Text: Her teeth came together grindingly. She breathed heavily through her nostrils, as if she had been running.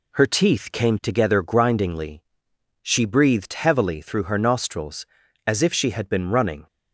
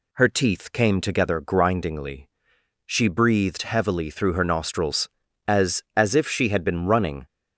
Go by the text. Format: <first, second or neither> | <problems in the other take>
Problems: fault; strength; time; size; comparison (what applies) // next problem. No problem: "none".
first | says "as" twice; at 5.9 s